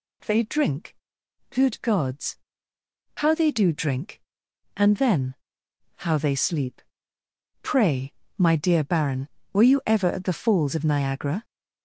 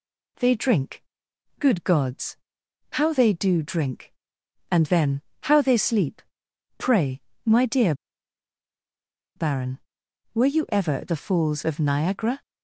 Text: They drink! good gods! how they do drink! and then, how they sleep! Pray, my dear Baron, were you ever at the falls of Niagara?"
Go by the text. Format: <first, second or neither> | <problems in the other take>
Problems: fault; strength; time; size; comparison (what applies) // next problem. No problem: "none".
first | pauses between "dear" and "Baron"; strong; at 7.9 s; 1.4 s long